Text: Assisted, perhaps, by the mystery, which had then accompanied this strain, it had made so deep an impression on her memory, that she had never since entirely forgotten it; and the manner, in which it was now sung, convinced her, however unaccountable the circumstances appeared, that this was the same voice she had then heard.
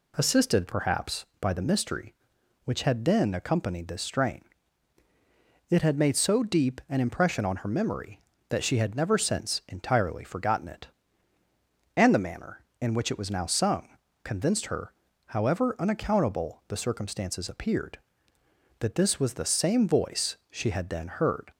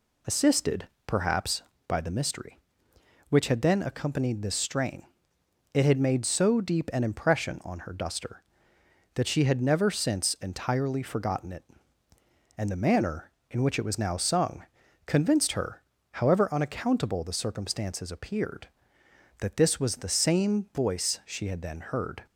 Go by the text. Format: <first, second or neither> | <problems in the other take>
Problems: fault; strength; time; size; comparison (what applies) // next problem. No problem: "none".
first | says "duster" for "memory"; at 7.9 s